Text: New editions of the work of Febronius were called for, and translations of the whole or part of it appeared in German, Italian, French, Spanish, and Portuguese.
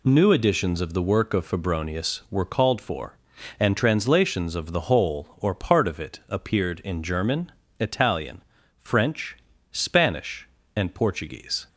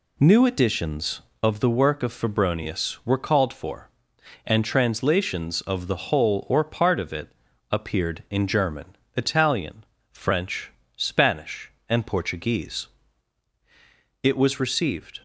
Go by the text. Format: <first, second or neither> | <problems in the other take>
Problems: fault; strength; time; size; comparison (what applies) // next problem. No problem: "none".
first | pauses between "it" and "appeared"; at 7.2 s; 0.44 s long // goes on to say "It was received"; noticeable; from 14.2 s on; 0.96 s long